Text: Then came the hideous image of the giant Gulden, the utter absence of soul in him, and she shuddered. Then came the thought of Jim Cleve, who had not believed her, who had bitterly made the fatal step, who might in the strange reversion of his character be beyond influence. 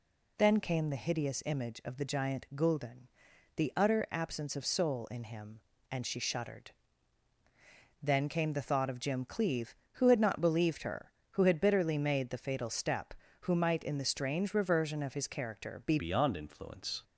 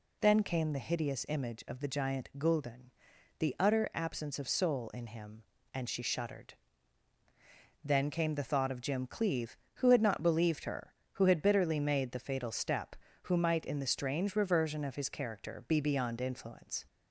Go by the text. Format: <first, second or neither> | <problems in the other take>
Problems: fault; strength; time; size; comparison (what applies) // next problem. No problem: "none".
second | changes voice at "beyond"; from 15.9 s on; 1.1 s long